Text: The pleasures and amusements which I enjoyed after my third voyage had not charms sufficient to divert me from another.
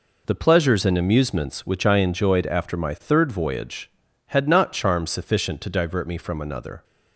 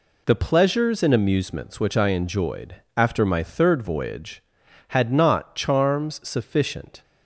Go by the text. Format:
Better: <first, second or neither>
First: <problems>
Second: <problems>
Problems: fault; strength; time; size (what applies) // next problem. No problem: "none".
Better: first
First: none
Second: pauses between "enjoyed" and "after"; slight; at 2.7 s; 0.20 s long // stops before "to divert me from another"; at 7.0 s